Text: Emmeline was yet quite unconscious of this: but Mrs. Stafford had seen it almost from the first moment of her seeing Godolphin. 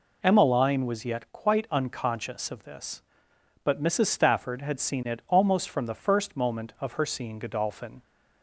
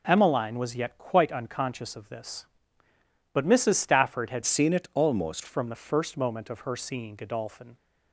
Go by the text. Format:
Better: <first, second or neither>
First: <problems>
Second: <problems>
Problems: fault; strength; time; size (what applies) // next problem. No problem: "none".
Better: first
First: none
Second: changes voice from "seen" to "almost"; from 4.4 to 5.4 s; 1.0 s long